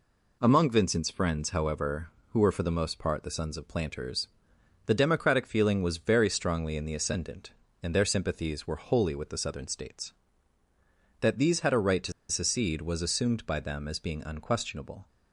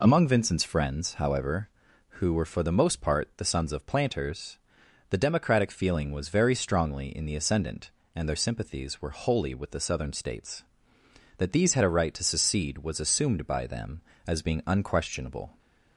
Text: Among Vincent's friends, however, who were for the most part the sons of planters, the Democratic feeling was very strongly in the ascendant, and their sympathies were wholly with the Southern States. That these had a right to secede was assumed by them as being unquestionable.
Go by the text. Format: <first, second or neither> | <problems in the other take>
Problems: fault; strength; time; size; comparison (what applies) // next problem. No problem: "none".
second | pauses between "to" and "secede"; slight; at 12.1 s; 0.17 s long